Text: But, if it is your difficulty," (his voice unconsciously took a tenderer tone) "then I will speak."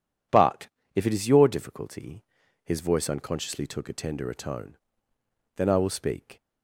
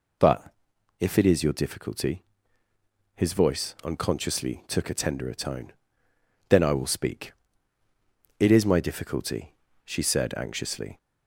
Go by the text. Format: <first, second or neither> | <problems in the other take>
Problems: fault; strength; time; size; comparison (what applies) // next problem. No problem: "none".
first | goes on to say "It is my difficulty she said anxiously"; strong; from 8.3 s on; 2.5 s long